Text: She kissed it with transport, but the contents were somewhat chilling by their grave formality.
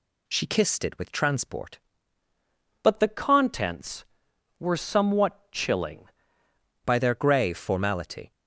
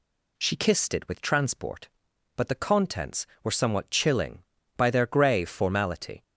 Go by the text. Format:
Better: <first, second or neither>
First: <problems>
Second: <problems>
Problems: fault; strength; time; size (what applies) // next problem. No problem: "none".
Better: second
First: changes voice from "but" to "chilling"; from 2.8 to 6.0 s; 3.2 s long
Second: none